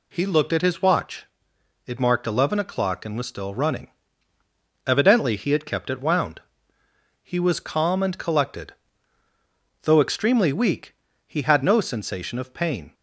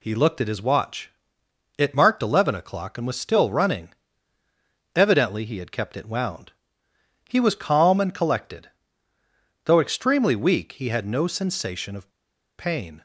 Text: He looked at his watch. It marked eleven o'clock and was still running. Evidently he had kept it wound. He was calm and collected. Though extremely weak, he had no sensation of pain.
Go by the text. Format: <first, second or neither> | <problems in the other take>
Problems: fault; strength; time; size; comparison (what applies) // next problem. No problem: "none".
first | pauses between "of" and "pain"; noticeable; at 12.1 s; 0.47 s long